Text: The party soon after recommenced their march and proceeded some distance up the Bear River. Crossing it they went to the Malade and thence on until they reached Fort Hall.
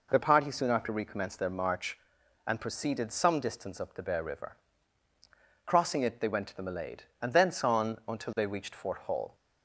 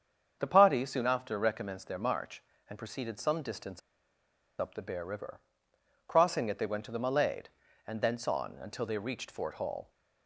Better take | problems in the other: first | starts louder than the rest; strong; until 1.4 s; 7 dB // pauses between "distance" and "up"; noticeable; at 3.8 s; 0.79 s long

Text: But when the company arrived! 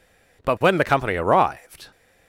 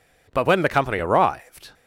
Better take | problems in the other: neither | none

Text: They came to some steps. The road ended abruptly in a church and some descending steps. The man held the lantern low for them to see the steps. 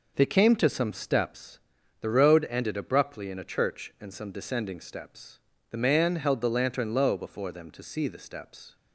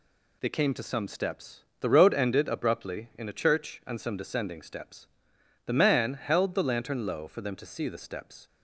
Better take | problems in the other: second | says "before" for "for"; at 7.1 s

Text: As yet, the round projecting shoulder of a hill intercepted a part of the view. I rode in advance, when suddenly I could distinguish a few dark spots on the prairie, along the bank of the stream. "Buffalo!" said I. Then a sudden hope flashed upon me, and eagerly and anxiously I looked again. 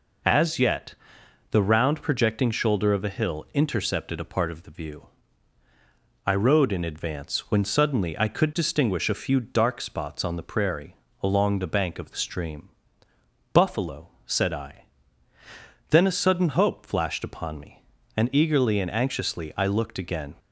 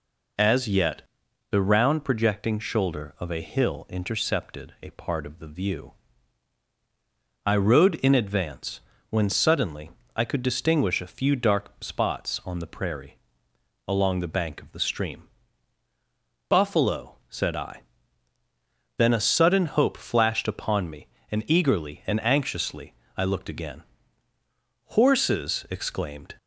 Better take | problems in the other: first | pauses between "suddenly" and "I"; slight; at 9.9 s; 0.26 s long // pauses between "anxiously" and "I"; slight; at 22.9 s; 0.24 s long // goes on to say "Horses exclaimed"; from 24.8 s on; 1.5 s long

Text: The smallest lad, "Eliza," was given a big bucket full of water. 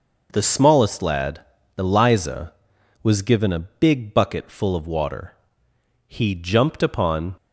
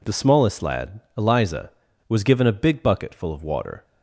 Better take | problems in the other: second | goes on to say "He jumped upon"; noticeable; from 6.0 s on; 1.2 s long

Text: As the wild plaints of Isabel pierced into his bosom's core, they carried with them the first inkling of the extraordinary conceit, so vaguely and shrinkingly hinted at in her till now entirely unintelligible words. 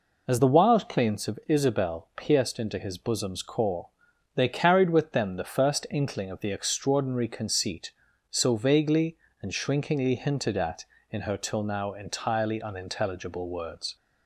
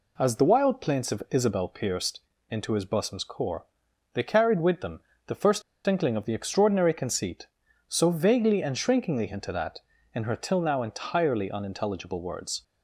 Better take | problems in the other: first | pauses between "pierced" and "into"; slight; at 2.2 s; 0.28 s long // pauses between "them" and "the"; slight; at 5.0 s; 0.26 s long // pauses between "first" and "inkling"; slight; at 5.6 s; 0.24 s long

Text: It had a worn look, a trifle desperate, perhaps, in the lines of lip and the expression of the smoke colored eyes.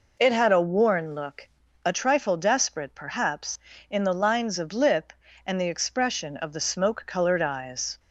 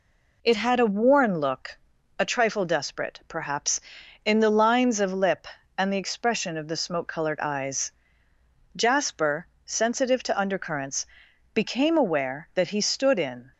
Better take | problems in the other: first | goes on to say "Jasper sensitive to undercurrents became aware that he stood in"; strong; from 8.7 s on; 4.7 s long

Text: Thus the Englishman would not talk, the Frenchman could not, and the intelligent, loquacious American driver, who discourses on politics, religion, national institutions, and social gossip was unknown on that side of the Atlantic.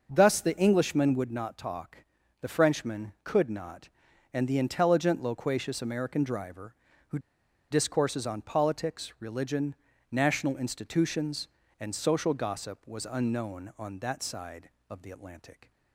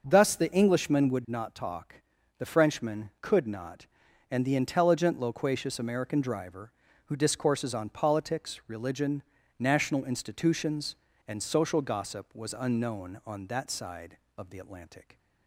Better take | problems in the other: second | pauses between "who" and "discourses"; noticeable; at 7.1 s; 0.52 s long

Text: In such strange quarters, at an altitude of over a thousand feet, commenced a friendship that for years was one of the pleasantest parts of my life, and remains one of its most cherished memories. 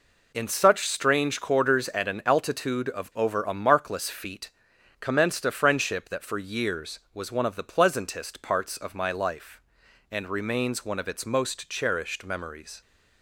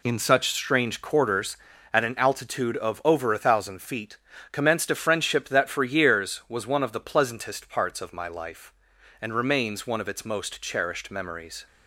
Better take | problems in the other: second | says "markless" for "thousand"; at 3.5 s

